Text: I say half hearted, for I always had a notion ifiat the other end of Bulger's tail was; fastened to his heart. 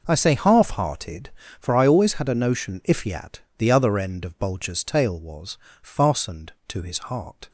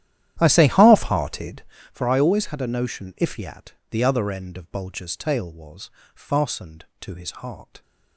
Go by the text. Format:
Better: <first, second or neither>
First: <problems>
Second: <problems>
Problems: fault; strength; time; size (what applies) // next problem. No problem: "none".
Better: first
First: pauses between "ifiat" and "the"; slight; at 3.3 s; 0.18 s long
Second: starts louder than the rest; strong; until 1.7 s; 11.5 dB // pauses between "ifiat" and "the"; slight; at 3.7 s; 0.18 s long